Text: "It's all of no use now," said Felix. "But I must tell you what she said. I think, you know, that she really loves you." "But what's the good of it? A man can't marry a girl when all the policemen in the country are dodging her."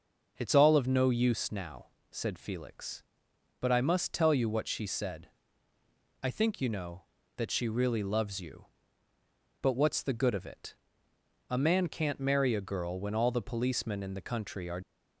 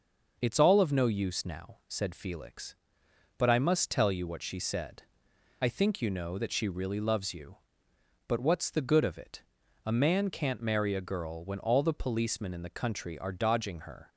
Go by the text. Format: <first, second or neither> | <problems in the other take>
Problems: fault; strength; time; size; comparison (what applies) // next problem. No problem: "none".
second | stops before "dodging her"; at 14.8 s